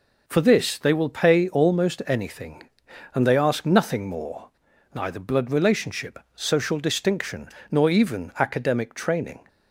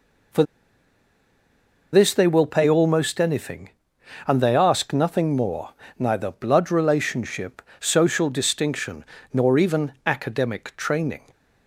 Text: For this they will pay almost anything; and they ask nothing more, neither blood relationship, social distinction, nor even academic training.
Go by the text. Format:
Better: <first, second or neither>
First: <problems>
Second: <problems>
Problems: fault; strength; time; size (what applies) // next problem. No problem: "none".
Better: first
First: none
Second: pauses between "For" and "this"; strong; at 0.4 s; 1.5 s long